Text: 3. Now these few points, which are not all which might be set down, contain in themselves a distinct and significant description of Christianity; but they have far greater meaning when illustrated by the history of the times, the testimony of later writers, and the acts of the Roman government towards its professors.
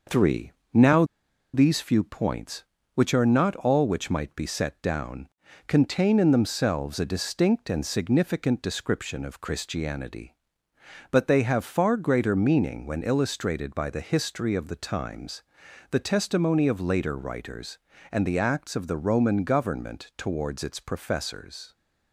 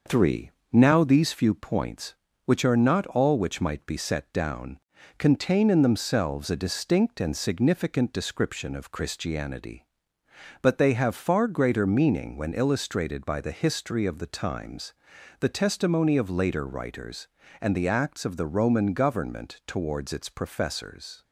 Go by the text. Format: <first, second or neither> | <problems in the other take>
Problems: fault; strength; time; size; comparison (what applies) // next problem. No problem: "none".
second | pauses between "Now" and "these"; noticeable; at 1.0 s; 0.49 s long